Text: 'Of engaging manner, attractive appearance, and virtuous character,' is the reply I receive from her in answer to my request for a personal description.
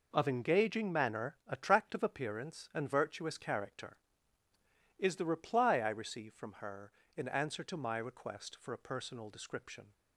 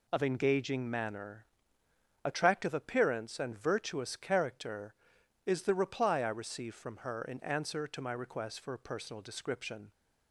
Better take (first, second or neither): neither